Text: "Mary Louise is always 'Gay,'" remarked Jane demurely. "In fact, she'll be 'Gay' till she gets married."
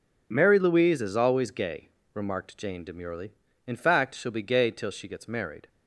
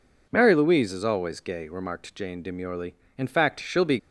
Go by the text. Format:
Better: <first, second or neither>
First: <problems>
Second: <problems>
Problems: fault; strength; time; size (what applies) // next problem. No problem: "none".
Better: first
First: none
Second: stops before "Gay till she gets married"; at 3.9 s